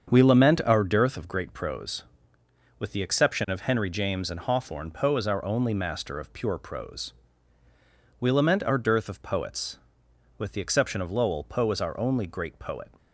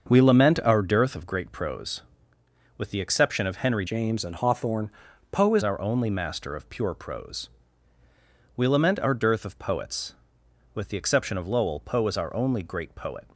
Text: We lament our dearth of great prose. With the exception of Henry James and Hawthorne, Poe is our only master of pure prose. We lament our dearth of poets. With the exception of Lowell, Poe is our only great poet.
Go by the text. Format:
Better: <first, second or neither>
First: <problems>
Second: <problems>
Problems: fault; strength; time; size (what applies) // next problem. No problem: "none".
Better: first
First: starts louder than the rest; strong; until 1.1 s; 7 dB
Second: starts louder than the rest; until 1.1 s; 6.5 dB // changes voice from "James" to "is"; from 3.8 to 5.6 s; 1.8 s long